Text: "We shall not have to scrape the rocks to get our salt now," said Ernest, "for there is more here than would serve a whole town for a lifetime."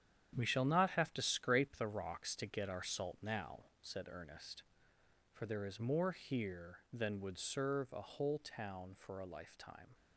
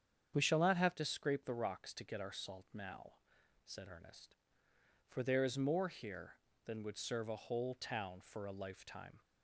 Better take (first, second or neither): second